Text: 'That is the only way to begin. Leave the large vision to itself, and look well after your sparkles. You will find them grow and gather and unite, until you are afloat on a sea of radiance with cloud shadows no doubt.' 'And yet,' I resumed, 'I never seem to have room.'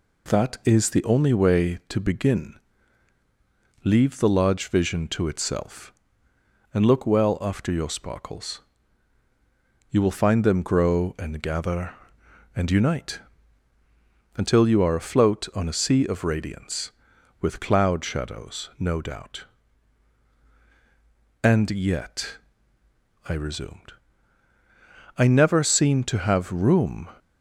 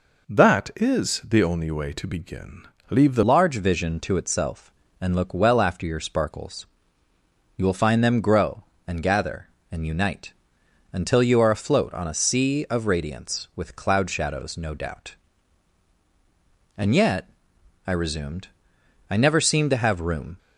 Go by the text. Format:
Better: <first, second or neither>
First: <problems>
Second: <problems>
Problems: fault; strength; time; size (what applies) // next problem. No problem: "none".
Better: first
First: none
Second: changes voice at "large"; from 3.2 s on; 17.1 s long